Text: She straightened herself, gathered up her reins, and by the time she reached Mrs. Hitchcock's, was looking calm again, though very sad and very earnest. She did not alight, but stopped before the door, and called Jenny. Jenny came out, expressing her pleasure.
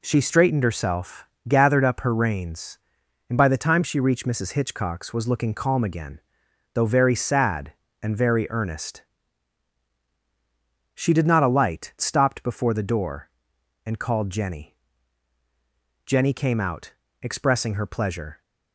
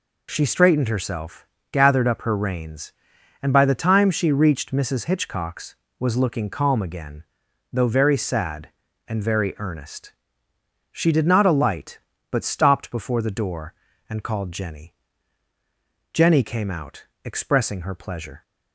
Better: second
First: skips "but"; at 11.9 s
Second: none

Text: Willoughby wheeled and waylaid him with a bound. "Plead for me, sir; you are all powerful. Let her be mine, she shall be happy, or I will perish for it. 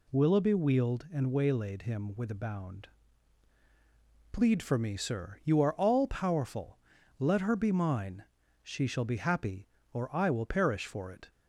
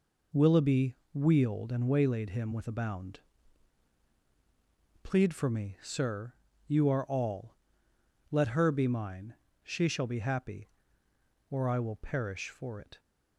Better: first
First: none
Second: pauses between "Willoughby" and "wheeled"; slight; at 0.9 s; 0.16 s long // skips "powerful"; at 7.9 s

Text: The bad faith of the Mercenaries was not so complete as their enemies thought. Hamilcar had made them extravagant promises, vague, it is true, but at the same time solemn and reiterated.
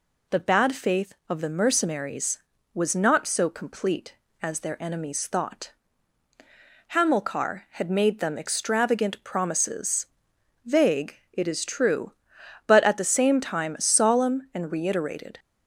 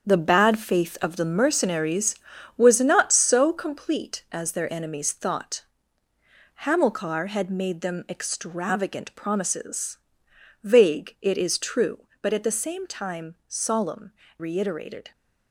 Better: first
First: none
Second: starts louder than the rest; strong; until 1.1 s; 7.5 dB // skips "and"; at 14.2 s

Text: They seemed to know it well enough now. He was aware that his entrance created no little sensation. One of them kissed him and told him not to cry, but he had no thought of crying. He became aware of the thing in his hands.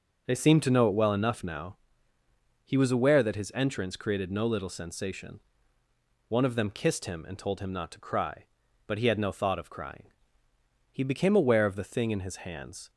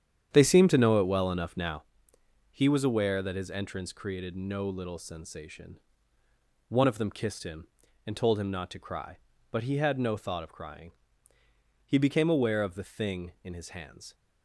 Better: first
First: none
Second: starts louder than the rest; strong; until 1.9 s; 9 dB

